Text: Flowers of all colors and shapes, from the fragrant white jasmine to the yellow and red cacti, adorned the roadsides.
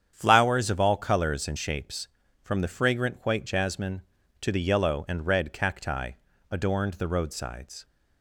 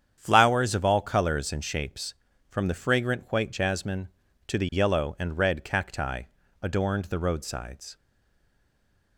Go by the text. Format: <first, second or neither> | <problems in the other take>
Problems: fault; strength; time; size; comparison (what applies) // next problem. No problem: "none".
first | starts louder than the rest; strong; until 1.1 s; 8.5 dB; strong in the first // stays silent after the last word; noticeable; from 7.9 s on; 1.2 s long